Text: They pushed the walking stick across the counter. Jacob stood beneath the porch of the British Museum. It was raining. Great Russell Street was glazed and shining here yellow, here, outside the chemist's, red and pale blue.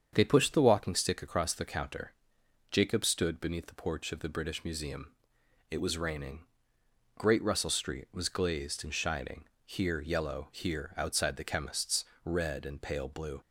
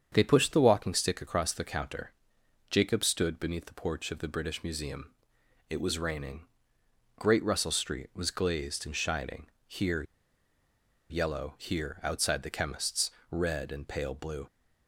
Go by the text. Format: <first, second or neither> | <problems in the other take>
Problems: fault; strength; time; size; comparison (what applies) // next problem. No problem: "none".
first | starts louder than the rest; strong; until 1.1 s; 7.5 dB; strong in the first // pauses between "shining" and "here"; slight; at 9.4 s; 0.20 s long; slight in the first // pauses between "here" and "yellow"; at 10.0 s; 1.0 s long